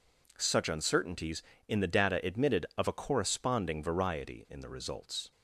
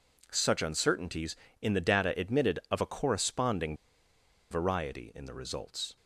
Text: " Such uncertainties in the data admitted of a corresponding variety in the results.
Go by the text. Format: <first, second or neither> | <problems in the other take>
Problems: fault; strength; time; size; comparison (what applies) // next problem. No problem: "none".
first | pauses between "corresponding" and "variety"; noticeable; at 3.7 s; 0.75 s long